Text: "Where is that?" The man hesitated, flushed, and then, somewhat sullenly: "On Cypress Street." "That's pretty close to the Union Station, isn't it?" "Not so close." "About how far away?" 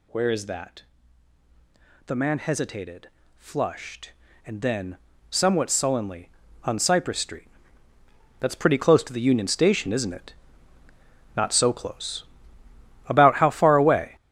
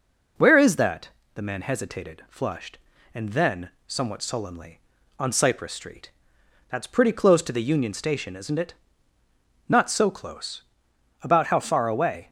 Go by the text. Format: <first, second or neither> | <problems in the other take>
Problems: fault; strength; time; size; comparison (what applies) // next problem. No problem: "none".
second | gets louder; strong; throughout; 10 dB